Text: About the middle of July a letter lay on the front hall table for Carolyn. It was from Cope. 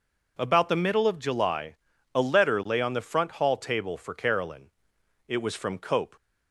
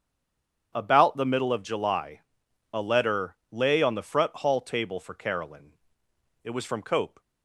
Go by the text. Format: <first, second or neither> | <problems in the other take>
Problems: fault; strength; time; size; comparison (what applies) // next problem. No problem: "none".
first | stays silent before the first word; slight; until 0.7 s; 0.7 s long // starts louder than the rest; strong; until 1.7 s; 7.5 dB // pauses between "July" and "a"; noticeable; at 2.1 s; 0.52 s long; slight in the first